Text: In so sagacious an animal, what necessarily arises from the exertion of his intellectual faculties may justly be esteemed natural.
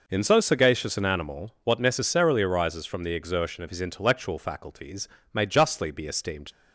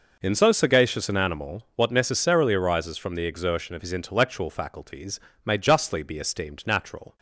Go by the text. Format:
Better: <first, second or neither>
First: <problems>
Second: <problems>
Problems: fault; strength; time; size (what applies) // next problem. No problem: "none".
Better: second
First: pauses between "faculties" and "may"; slight; at 5.0 s; 0.26 s long // stops before "natural"; at 6.5 s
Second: pauses between "faculties" and "may"; slight; at 5.1 s; 0.26 s long